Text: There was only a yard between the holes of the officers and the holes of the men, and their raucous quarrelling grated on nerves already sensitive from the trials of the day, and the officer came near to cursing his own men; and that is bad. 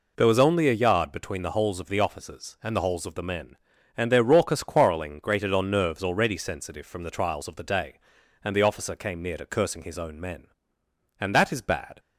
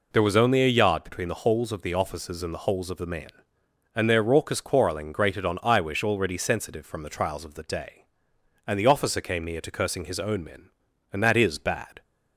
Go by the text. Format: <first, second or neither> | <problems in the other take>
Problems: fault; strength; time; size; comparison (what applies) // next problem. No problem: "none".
first | says "iwish" for "nerves"; at 5.5 s